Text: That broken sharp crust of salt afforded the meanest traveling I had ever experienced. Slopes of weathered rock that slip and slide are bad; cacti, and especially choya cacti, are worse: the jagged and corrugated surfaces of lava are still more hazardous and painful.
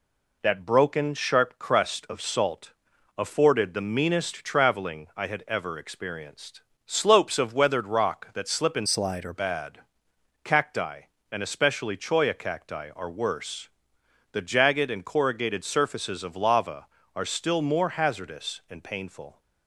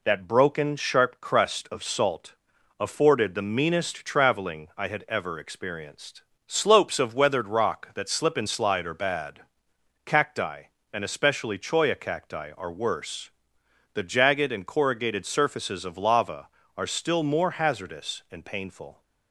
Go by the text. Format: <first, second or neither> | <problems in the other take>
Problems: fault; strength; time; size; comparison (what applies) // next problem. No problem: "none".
second | pauses between "salt" and "afforded"; noticeable; at 2.7 s; 0.46 s long; noticeable in the second // changes voice from "slide" to "are"; from 8.8 to 9.3 s; 0.5 s long